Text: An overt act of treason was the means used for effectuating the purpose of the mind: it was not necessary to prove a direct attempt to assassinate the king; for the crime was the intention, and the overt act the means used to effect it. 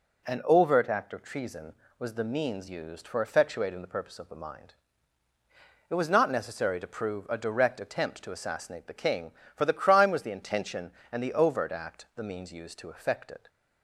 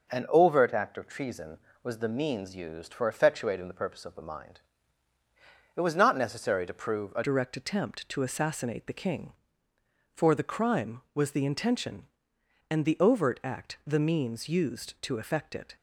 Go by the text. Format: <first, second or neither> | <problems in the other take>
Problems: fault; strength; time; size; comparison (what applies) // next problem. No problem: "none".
first | changes voice at "direct"; from 7.2 s on; 8.5 s long